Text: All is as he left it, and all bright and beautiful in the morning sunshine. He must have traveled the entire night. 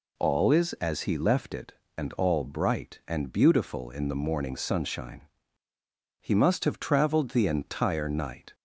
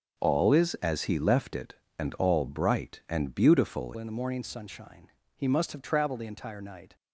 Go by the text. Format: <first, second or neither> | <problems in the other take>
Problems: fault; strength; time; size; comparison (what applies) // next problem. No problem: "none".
first | changes voice at "in"; from 3.9 s on; 3.0 s long